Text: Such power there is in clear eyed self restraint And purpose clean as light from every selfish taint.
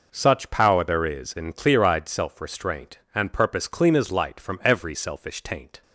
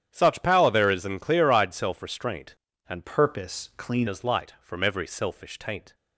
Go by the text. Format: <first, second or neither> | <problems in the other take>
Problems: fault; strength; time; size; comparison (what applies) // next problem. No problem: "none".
first | starts louder than the rest; strong; until 1.1 s; 9.5 dB // changes voice from "purpose" to "clean"; from 3.0 to 4.0 s; 1.0 s long